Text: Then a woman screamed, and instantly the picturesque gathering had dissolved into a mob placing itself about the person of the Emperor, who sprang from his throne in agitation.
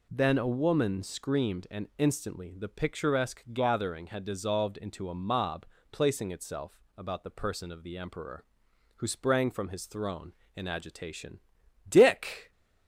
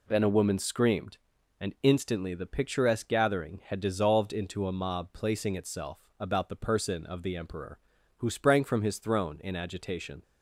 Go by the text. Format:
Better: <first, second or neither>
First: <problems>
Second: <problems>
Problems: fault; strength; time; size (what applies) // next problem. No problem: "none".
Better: second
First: pauses between "mob" and "placing"; slight; at 5.6 s; 0.26 s long // pauses between "itself" and "about"; slight; at 6.7 s; 0.18 s long // goes on to say "Dick"; noticeable; from 11.8 s on; 0.64 s long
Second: pauses between "itself" and "about"; slight; at 5.9 s; 0.22 s long